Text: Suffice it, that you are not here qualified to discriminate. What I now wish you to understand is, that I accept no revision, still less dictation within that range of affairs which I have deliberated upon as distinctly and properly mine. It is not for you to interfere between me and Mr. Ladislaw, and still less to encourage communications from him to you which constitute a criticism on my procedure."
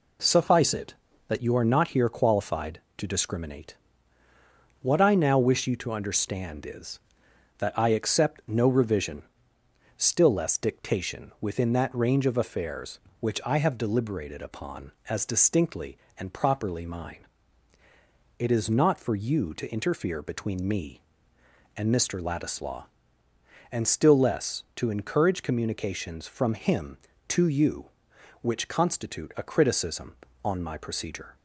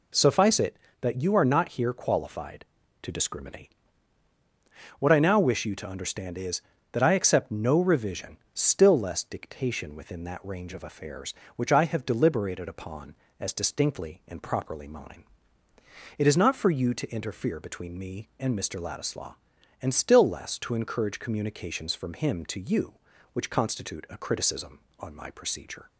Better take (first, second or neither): neither